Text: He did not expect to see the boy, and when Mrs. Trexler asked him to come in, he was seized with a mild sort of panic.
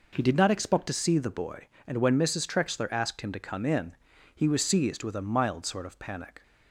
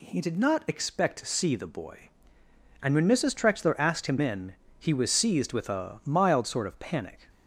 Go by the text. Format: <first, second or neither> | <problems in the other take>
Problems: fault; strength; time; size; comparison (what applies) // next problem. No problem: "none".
first | skips "to come"; at 4.1 s